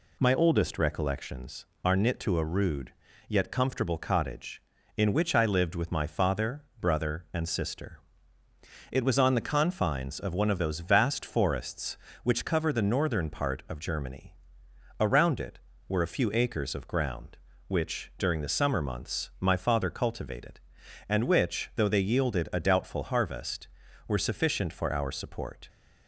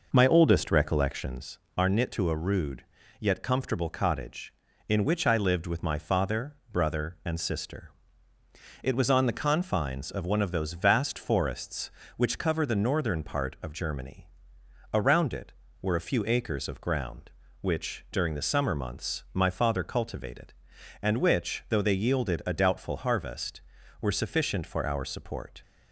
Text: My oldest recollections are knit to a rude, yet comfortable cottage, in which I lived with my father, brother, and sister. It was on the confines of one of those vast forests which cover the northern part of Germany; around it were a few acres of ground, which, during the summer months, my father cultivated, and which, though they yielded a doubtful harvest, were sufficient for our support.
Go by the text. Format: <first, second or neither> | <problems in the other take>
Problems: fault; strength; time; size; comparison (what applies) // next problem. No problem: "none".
first | starts louder than the rest; noticeable; until 1.5 s; 5 dB